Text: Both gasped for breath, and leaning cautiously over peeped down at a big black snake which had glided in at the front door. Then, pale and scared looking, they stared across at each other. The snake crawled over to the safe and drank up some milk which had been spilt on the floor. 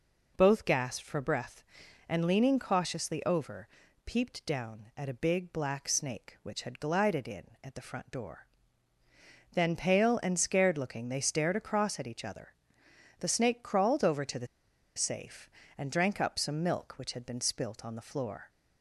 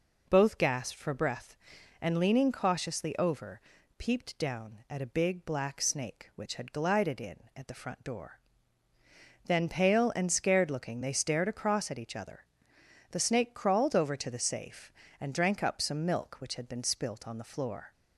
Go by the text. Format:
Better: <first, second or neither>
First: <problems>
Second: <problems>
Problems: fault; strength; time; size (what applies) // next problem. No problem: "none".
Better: second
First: pauses between "over" and "peeped"; slight; at 3.6 s; 0.36 s long // pauses between "the" and "safe"; noticeable; at 14.4 s; 0.50 s long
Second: pauses between "over" and "peeped"; slight; at 3.6 s; 0.36 s long